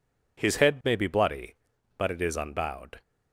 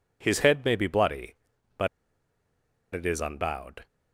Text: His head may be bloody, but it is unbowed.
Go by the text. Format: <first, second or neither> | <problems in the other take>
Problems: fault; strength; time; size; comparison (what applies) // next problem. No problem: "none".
first | pauses between "but" and "it"; at 1.8 s; 1.0 s long